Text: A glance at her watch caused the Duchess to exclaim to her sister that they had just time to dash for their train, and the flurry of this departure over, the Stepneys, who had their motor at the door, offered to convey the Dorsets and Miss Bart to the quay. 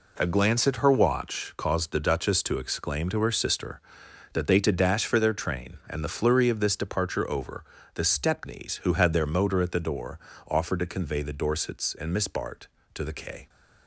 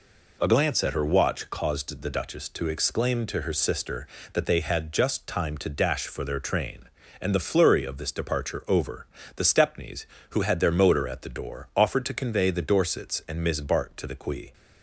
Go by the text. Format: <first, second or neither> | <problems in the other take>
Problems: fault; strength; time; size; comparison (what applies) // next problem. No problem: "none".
second | skips "had just time"; at 4.5 s